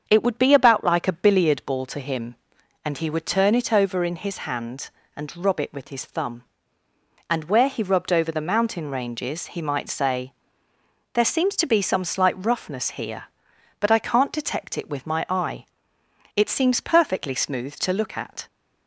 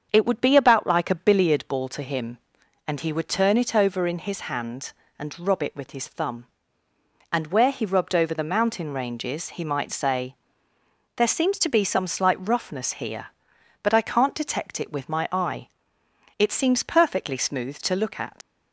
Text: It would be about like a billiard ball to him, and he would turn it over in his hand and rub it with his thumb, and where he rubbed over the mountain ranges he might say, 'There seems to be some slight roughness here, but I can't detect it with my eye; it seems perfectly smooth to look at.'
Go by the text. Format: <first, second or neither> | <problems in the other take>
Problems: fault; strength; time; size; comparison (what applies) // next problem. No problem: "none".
first | starts louder than the rest; strong; until 1.1 s; 7 dB; strong in the first // leaves "at" unfinished; at 18.4 s; 80 ms